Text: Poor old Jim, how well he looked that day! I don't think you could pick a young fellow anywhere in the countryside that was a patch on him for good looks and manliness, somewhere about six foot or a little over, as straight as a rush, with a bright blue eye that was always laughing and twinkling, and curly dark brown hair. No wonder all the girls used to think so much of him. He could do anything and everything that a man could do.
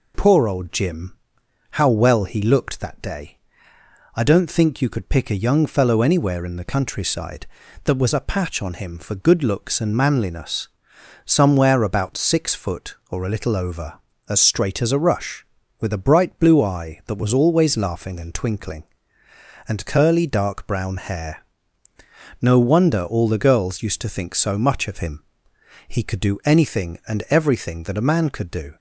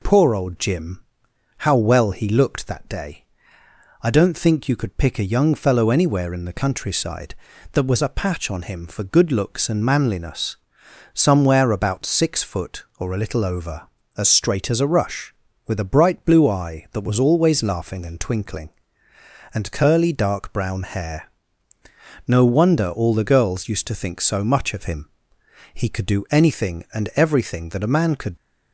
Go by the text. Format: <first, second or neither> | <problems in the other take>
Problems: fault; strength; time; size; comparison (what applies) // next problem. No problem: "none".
first | stops before "do"; at 28.3 s